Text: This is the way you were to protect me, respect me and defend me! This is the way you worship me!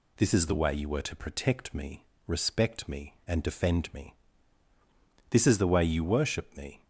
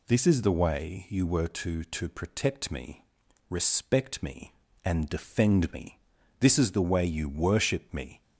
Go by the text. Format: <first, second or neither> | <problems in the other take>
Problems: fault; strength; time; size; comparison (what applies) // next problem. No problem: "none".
first | says "to" twice; at 1.8 s